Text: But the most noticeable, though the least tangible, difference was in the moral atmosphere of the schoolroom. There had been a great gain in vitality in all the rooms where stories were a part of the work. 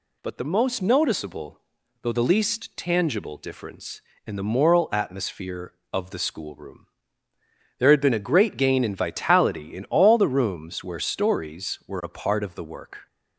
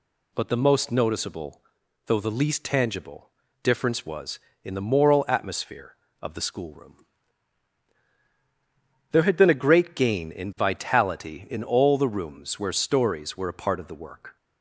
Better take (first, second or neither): second